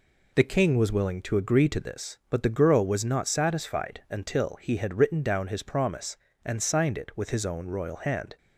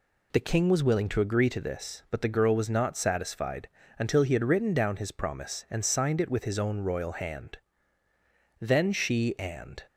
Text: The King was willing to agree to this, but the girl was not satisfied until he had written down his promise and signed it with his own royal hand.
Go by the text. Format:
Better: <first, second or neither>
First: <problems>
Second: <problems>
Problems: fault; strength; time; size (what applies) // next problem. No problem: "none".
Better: first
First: none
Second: pauses between "satisfied" and "until"; slight; at 3.6 s; 0.30 s long // goes on to say "Then she and"; noticeable; from 8.6 s on; 1.2 s long